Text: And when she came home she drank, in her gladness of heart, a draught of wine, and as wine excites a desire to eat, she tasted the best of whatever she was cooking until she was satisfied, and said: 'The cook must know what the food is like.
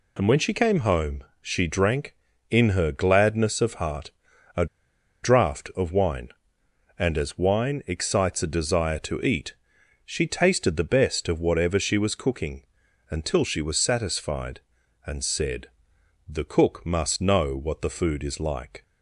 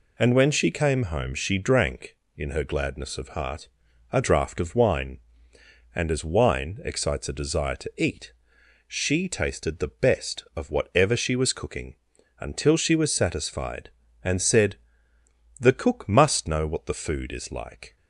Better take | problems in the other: second | pauses between "home" and "she"; slight; at 1.2 s; 0.18 s long // pauses between "a" and "draught"; noticeable; at 4.6 s; 0.57 s long // pauses between "cooking" and "until"; noticeable; at 12.6 s; 0.48 s long; noticeable in the second

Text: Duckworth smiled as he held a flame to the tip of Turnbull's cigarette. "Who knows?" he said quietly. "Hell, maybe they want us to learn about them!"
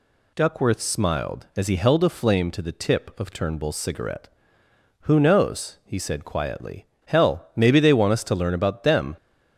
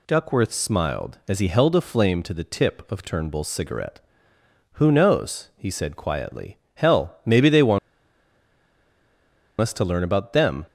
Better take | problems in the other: first | pauses between "want" and "us"; strong; at 7.7 s; 1.8 s long

